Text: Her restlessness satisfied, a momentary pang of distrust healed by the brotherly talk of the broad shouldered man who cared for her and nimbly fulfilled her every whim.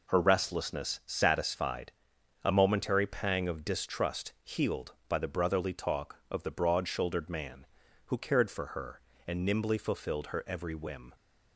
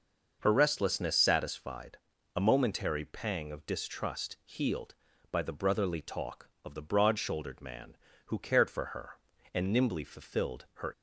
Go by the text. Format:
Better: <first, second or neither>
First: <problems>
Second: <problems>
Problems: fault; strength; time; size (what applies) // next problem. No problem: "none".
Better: first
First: none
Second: stops before "every whim"; at 10.9 s